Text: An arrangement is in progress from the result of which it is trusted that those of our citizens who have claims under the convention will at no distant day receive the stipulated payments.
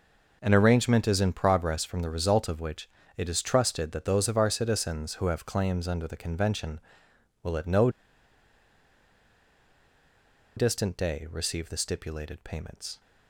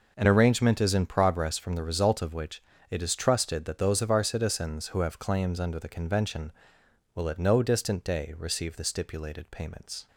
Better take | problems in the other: second | pauses between "which" and "it"; slight; at 2.8 s; 0.28 s long; slight in the second // pauses between "no" and "distant"; strong; at 7.8 s; 2.6 s long

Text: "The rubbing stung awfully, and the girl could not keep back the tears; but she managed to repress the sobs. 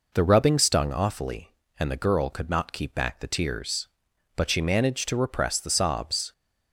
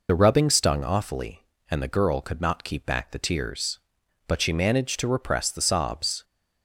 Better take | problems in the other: first | loses the start of "The"; at 0.0 s; 40 ms

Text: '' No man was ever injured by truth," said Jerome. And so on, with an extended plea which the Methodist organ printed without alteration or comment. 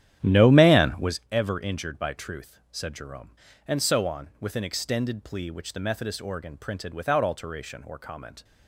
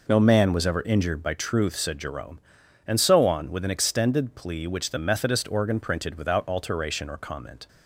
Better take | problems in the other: second | starts louder than the rest; strong; until 1.2 s; 11.5 dB

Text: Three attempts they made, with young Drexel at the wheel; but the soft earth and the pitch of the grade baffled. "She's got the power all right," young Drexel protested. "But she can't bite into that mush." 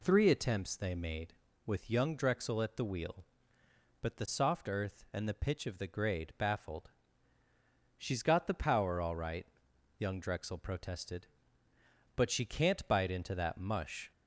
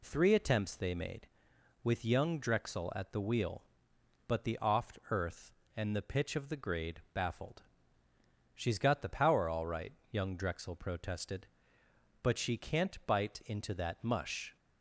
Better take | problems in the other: first | says "oft" for "soft"; at 4.6 s

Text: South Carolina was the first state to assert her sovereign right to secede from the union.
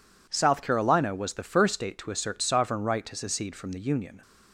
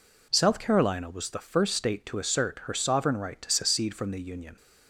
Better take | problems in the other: second | skips "her"; at 2.4 s

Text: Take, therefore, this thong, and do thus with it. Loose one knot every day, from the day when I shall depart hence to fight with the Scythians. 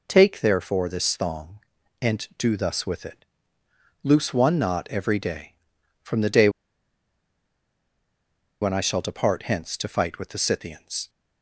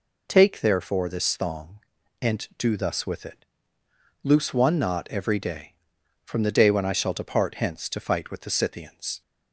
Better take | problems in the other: second | pauses between "day" and "when"; strong; at 6.4 s; 2.1 s long

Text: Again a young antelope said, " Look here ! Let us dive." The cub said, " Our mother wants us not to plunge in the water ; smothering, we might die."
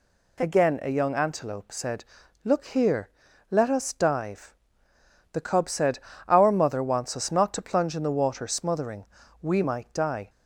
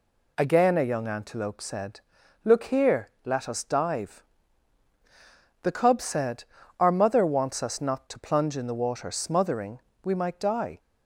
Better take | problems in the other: neither | none

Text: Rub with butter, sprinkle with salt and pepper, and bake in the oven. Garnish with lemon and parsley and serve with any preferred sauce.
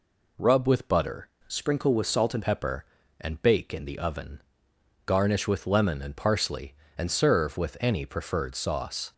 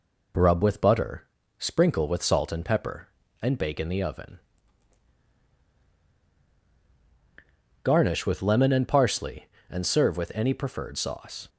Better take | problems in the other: second | changes voice from "sprinkle" to "and"; from 1.4 to 2.4 s; 1.0 s long

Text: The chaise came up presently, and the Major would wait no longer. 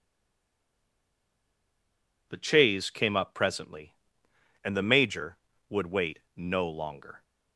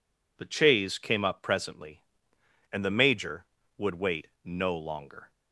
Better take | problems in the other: second | stays silent before the first word; until 2.2 s; 2.2 s long // pauses between "wait" and "no"; slight; at 6.1 s; 0.16 s long; slight in the second

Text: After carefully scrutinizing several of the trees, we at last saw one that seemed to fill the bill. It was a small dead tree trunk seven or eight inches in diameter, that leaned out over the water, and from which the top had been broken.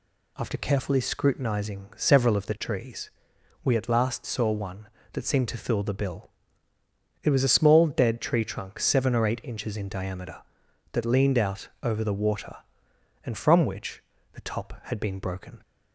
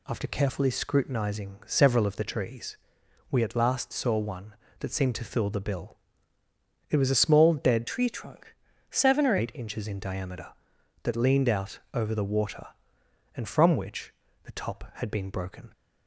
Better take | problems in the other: first | changes voice from "tree" to "or"; from 7.8 to 9.3 s; 1.5 s long // pauses between "trunk" and "seven"; slight; at 8.5 s; 0.36 s long // pauses between "which" and "the"; slight; at 14.1 s; 0.32 s long; slight in the first

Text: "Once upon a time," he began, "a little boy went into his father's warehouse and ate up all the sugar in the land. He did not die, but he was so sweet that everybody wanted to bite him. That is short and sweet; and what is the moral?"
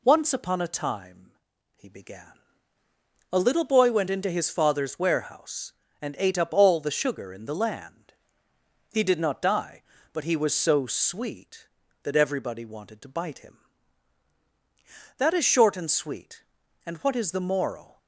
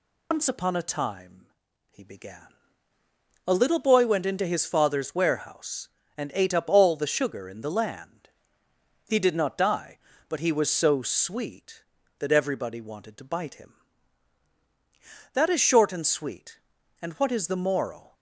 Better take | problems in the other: first | loses the start of "Once"; at 0.3 s; 120 ms

